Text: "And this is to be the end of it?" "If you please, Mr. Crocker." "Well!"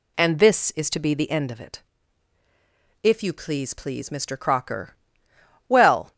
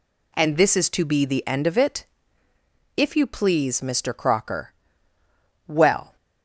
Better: second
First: says "please" twice; at 3.7 s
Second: none

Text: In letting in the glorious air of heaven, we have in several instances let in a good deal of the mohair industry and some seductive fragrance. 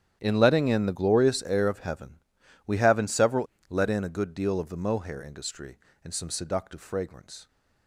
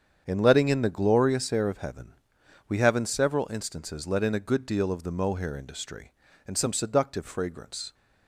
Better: second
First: starts louder than the rest; strong; until 1.2 s; 10 dB // skips "instances"; at 3.5 s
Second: starts louder than the rest; strong; until 1.2 s; 8 dB

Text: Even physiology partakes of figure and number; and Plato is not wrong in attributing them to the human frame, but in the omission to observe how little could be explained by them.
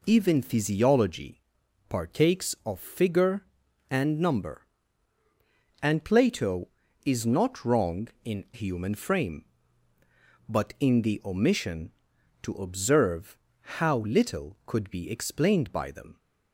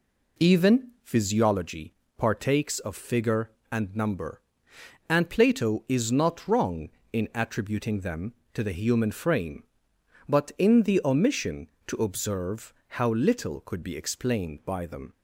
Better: second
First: pauses between "physiology" and "partakes"; noticeable; at 1.4 s; 0.48 s long // skips "attributing them to the"; at 8.4 s // pauses between "observe" and "how"; at 13.3 s; 0.40 s long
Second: pauses between "physiology" and "partakes"; slight; at 1.9 s; 0.24 s long // pauses between "observe" and "how"; slight; at 12.7 s; 0.26 s long

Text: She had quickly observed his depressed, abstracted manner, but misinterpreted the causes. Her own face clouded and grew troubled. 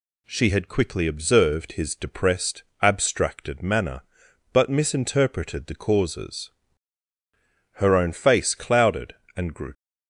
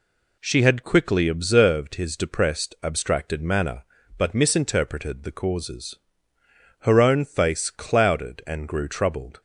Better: second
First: stops before "troubled"; at 9.7 s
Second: none

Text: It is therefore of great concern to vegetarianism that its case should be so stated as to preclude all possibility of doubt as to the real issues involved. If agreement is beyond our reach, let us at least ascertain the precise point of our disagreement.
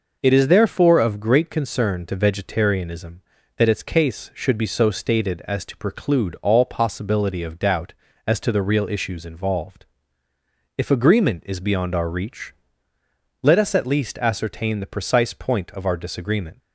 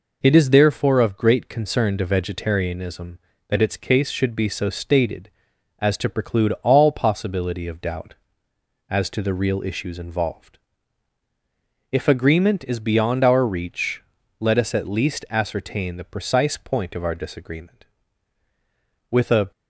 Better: first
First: none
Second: goes on to say "With a"; slight; from 19.0 s on; 0.42 s long

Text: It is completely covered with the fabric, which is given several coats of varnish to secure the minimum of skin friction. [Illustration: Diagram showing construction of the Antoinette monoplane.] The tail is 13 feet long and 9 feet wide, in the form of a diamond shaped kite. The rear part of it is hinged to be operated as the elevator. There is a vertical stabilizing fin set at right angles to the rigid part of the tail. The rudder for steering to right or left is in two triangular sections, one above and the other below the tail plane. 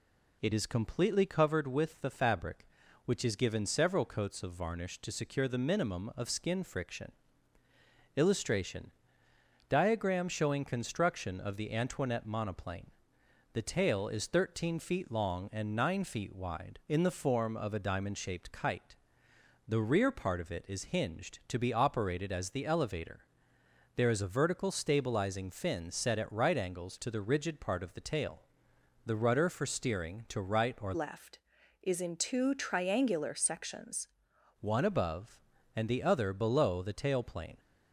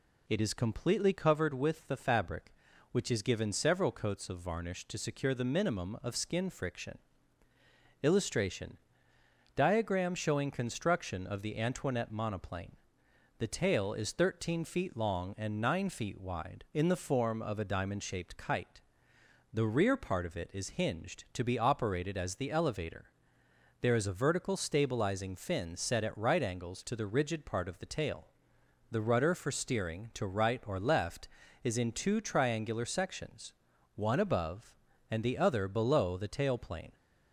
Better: second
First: changes voice from "left" to "sections"; from 30.9 to 34.0 s; 3.1 s long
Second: none

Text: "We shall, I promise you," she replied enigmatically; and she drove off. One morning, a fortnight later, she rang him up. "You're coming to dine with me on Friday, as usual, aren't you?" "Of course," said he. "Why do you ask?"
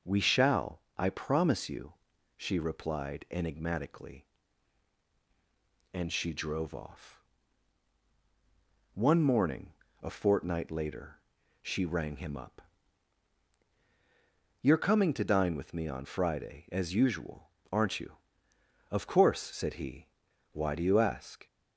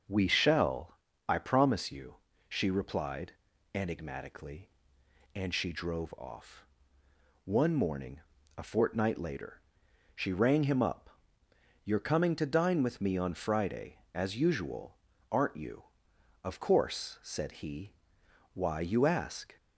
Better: first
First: none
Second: starts louder than the rest; until 1.3 s; 6 dB // pauses between "replied" and "enigmatically"; at 3.3 s; 0.42 s long // skips "do"; at 18.7 s

